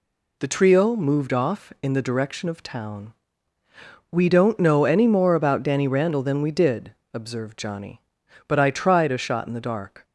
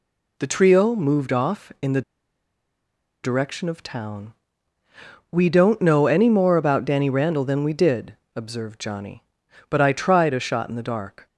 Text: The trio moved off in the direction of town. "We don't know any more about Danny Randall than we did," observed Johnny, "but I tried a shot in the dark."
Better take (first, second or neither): first